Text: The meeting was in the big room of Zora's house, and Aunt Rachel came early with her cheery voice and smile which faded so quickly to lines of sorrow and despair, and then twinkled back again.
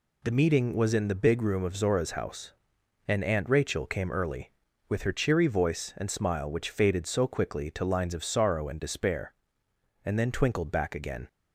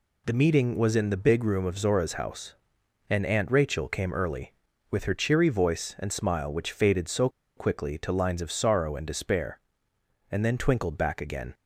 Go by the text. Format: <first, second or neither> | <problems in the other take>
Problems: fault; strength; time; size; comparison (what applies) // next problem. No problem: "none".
first | pauses between "so" and "quickly"; slight; at 7.2 s; 0.28 s long